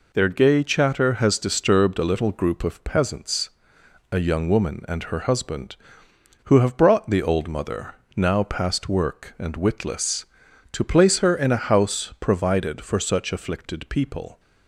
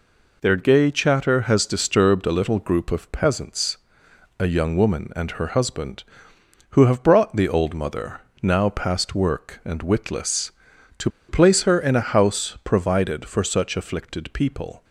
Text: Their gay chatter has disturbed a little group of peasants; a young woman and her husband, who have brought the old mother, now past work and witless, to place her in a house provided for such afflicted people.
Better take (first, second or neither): first